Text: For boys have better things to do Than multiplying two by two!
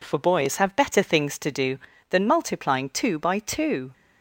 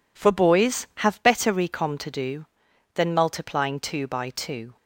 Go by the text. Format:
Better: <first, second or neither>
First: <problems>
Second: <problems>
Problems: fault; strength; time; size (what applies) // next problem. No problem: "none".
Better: first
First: none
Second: says "recom" for "things"; at 1.5 s